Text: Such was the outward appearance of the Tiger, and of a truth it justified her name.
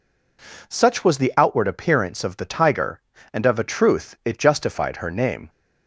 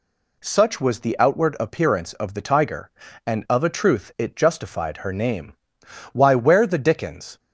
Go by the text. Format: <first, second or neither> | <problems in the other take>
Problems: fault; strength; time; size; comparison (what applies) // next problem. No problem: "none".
first | goes on to say "Why where the dickens"; noticeable; from 6.1 s on; 1.2 s long